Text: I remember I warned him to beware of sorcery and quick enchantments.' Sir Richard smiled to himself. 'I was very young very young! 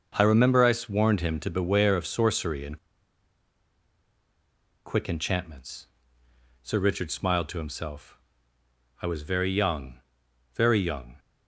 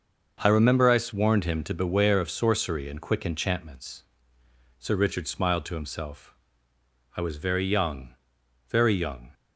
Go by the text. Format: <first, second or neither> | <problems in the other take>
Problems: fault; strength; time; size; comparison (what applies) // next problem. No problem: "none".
second | starts louder than the rest; until 1.3 s; 6.5 dB; also in the second // pauses between "and" and "quick"; strong; at 2.7 s; 2.0 s long // pauses between "young" and "very"; noticeable; at 9.9 s; 0.58 s long; noticeable in the second